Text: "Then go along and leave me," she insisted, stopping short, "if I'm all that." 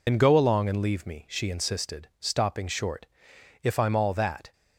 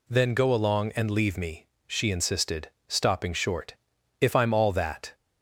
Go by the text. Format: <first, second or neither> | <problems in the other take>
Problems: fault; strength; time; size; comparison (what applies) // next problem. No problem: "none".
second | loses the start of "Then"; at 0.0 s; 70 ms